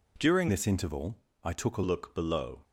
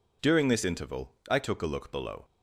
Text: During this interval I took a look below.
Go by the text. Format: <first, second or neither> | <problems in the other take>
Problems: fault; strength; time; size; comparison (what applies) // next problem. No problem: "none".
second | changes voice from "this" to "a"; from 0.4 to 1.8 s; 1.4 s long // pauses between "interval" and "I"; slight; at 1.1 s; 0.26 s long; slight in the second